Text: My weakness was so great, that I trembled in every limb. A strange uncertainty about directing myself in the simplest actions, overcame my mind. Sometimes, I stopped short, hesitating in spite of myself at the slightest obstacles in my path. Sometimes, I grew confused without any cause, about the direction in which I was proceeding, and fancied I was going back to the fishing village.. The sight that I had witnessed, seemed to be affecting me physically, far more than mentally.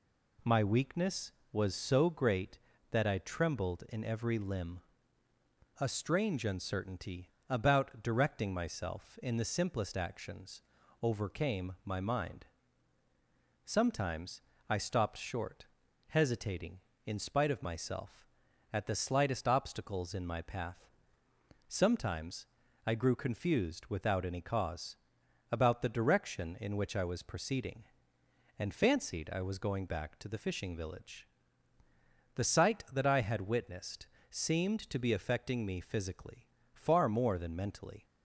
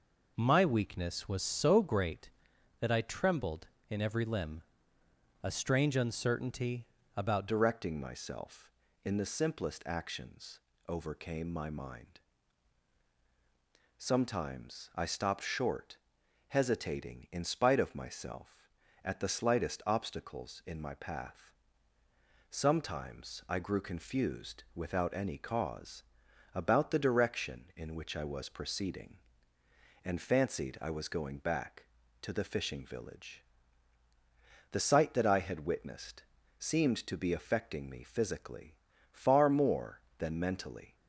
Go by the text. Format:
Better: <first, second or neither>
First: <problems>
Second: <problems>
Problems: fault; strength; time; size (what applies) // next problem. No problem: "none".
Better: first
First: pauses between "uncertainty" and "about"; slight; at 7.2 s; 0.20 s long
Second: pauses between "uncertainty" and "about"; slight; at 6.8 s; 0.32 s long // changes voice at "directing"; from 7.4 s on; 33.5 s long